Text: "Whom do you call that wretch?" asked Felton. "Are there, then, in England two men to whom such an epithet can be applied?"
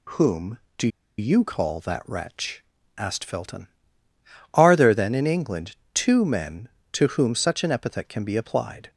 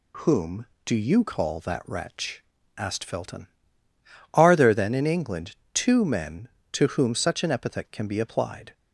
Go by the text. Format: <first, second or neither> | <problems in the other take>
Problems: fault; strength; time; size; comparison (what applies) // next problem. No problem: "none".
second | pauses between "do" and "you"; slight; at 0.8 s; 0.30 s long // pauses between "England" and "two"; slight; at 5.7 s; 0.18 s long; slight in the second